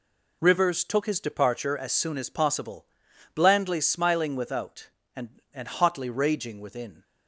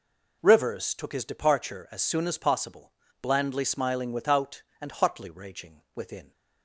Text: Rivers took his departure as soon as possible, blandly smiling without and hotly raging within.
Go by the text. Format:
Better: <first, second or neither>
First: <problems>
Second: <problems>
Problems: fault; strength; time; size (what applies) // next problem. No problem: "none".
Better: second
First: says "and" twice; at 5.5 s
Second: none